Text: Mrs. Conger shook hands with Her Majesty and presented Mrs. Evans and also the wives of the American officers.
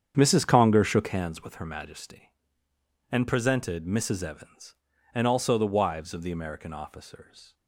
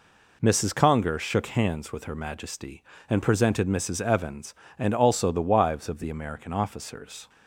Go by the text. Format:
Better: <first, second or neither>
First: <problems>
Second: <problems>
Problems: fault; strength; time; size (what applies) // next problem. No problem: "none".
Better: second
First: starts louder than the rest; strong; until 1.1 s; 8 dB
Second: none